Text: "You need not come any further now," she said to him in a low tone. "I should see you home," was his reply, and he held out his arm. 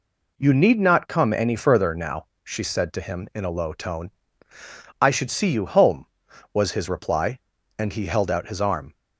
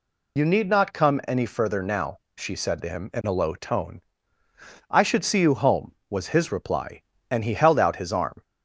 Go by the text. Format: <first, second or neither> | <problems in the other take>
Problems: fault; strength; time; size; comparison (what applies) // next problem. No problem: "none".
first | loses the start of "You"; at 0.3 s; 75 ms